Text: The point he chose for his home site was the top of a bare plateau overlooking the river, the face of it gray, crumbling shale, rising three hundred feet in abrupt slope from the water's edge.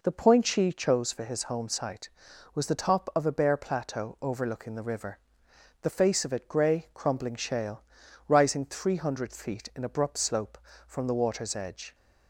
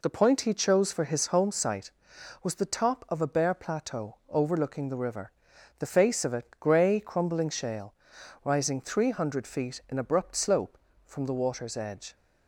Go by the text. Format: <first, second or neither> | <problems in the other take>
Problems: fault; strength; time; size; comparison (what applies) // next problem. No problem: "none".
second | says "she" for "he"; at 0.4 s